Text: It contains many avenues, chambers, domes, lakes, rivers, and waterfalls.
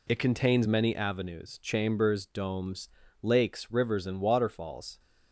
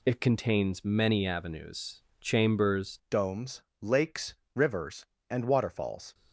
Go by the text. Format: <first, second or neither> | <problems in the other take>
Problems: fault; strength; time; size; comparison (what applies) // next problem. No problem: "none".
first | changes voice at "domes"; from 3.0 s on; 3.1 s long